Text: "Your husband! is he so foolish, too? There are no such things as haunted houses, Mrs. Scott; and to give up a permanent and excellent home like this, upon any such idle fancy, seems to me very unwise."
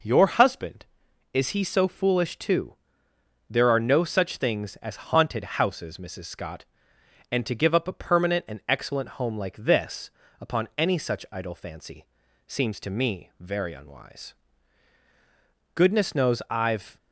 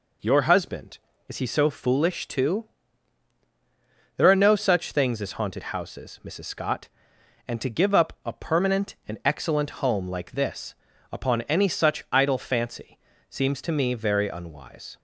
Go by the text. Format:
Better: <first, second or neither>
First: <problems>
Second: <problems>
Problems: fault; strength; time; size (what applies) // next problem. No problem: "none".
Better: second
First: goes on to say "Goodness knows I've"; noticeable; from 15.7 s on; 1.2 s long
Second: none